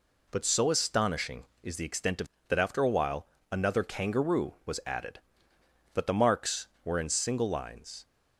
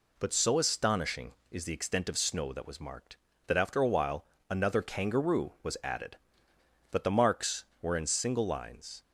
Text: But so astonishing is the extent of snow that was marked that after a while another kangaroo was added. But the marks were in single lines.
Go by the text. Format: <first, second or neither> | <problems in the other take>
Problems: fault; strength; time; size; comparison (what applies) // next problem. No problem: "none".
second | skips "snow that was marked"; at 2.3 s // pauses between "while" and "another"; slight; at 3.2 s; 0.26 s long; slight in the second